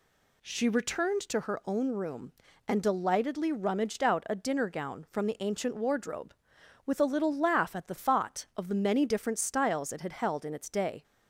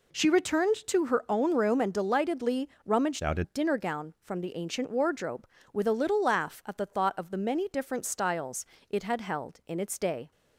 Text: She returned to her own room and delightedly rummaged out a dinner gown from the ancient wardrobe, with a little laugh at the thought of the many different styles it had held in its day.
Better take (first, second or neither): first